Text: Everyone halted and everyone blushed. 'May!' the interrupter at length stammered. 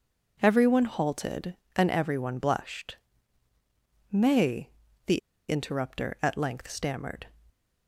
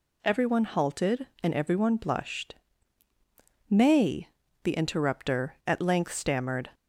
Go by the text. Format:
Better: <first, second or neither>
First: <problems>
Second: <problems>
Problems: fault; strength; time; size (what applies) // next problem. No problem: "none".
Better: second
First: pauses between "the" and "interrupter"; slight; at 5.1 s; 0.29 s long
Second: none